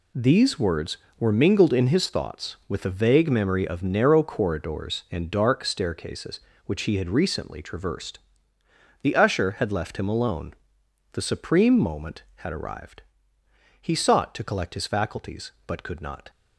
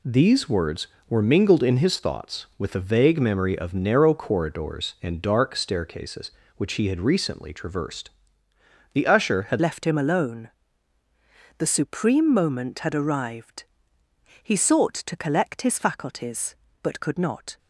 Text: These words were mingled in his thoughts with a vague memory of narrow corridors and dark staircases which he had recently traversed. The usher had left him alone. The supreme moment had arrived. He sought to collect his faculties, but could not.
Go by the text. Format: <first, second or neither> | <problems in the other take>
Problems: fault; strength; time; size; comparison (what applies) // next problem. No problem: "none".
first | changes voice at "left"; from 9.5 s on; 8.0 s long